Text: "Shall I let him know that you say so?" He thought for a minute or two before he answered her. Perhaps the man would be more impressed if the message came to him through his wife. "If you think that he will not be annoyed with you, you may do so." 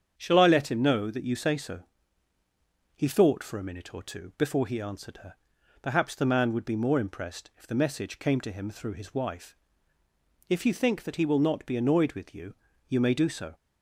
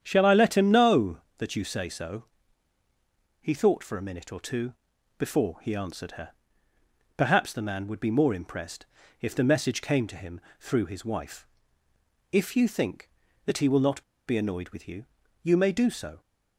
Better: first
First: starts louder than the rest; strong; until 1.1 s; 8 dB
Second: starts louder than the rest; strong; until 1.0 s; 9 dB // pauses between "two" and "before"; at 4.7 s; 0.44 s long // pauses between "impressed" and "if"; slight; at 8.8 s; 0.34 s long // pauses between "him" and "through"; slight; at 10.3 s; 0.20 s long // pauses between "not" and "be"; slight; at 14.0 s; 0.25 s long

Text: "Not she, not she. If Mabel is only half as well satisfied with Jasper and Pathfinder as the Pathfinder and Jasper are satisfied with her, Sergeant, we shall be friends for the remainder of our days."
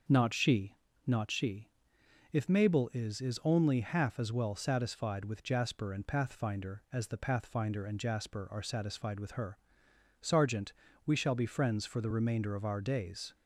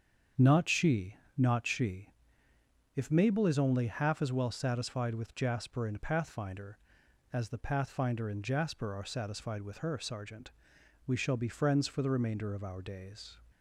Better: second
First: starts louder than the rest; until 1.3 s; 6.5 dB // says "is" twice; at 3.1 s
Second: starts louder than the rest; strong; until 1.5 s; 7.5 dB

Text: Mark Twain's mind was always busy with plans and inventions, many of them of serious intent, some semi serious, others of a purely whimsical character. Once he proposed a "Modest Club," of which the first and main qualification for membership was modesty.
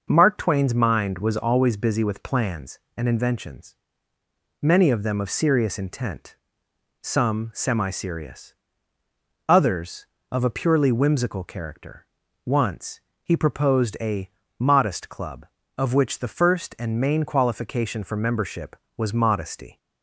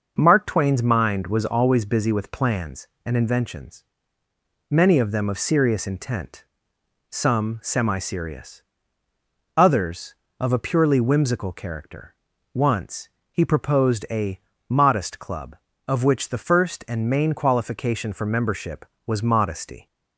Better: neither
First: pauses between "Once" and "he"; slight; at 13.0 s; 0.22 s long // pauses between "a" and "Modest"; slight; at 14.2 s; 0.28 s long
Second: pauses between "Once" and "he"; slight; at 13.0 s; 0.22 s long // pauses between "a" and "Modest"; slight; at 14.3 s; 0.28 s long

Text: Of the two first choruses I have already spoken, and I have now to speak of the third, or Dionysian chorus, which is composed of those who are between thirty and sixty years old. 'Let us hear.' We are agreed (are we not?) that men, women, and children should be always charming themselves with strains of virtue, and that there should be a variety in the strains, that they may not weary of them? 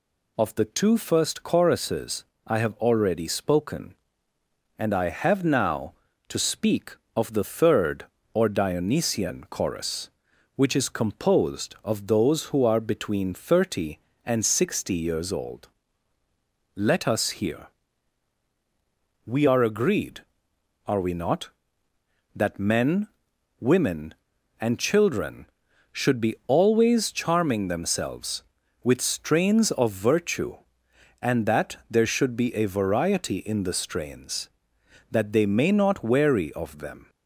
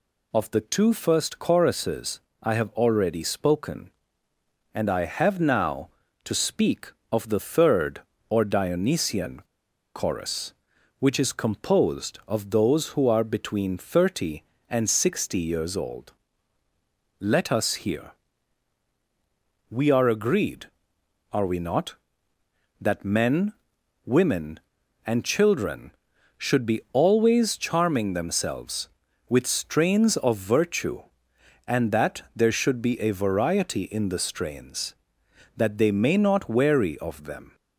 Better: first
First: pauses between "choruses" and "I"; slight; at 2.2 s; 0.24 s long // pauses between "that" and "there"; slight; at 31.7 s; 0.16 s long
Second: pauses between "choruses" and "I"; slight; at 2.1 s; 0.24 s long // pauses between "Dionysian" and "chorus"; noticeable; at 9.4 s; 0.53 s long // pauses between "that" and "there"; slight; at 32.2 s; 0.16 s long

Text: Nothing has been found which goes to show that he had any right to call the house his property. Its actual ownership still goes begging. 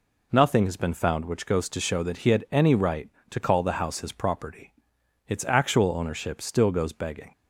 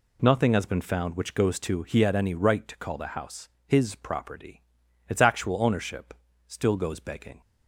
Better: first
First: none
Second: skips "show that"; at 1.8 s // pauses between "house" and "his"; slight; at 3.4 s; 0.18 s long // pauses between "ownership" and "still"; slight; at 6.1 s; 0.34 s long

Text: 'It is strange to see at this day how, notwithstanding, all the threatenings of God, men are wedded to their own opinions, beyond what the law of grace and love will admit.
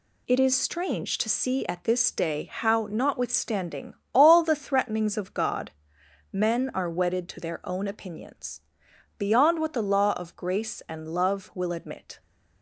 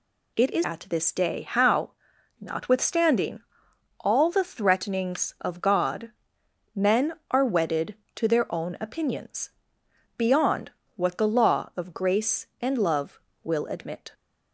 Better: first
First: none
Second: skips "strange to see"; at 0.6 s // pauses between "beyond" and "what"; slight; at 10.7 s; 0.26 s long

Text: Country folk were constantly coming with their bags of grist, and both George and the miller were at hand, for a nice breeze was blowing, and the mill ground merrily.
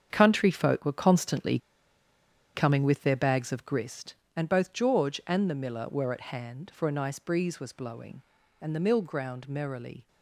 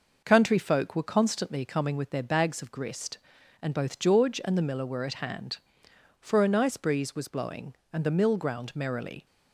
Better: second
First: starts louder than the rest; strong; until 1.1 s; 7.5 dB // pauses between "constantly" and "coming"; noticeable; at 1.5 s; 0.97 s long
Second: none

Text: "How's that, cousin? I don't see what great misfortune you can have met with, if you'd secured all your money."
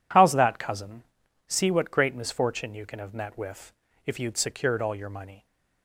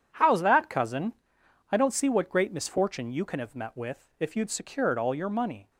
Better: second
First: skips "I don't"; at 1.2 s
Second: none

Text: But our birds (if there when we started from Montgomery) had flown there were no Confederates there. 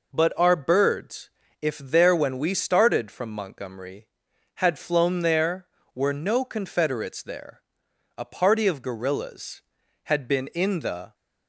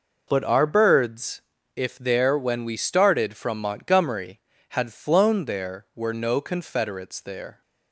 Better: second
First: goes on to say "A party of guerrillas had been in the"; strong; from 8.1 s on; 2.9 s long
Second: none

